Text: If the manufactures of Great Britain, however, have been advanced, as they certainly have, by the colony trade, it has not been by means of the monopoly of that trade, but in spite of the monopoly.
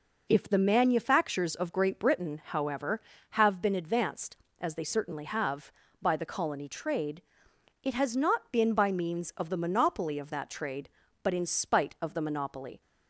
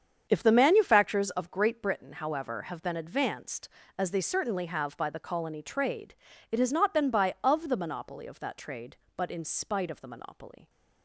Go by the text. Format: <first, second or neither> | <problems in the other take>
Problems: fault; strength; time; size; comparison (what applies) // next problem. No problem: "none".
first | starts louder than the rest; strong; until 1.3 s; 7.5 dB // skips "means"; at 7.3 s